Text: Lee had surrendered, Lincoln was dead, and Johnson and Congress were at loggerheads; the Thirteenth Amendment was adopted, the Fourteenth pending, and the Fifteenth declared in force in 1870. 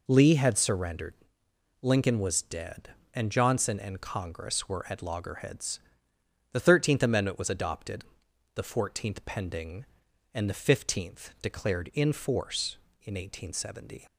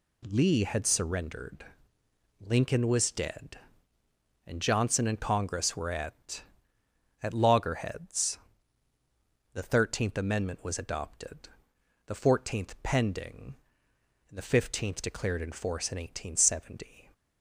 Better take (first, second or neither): first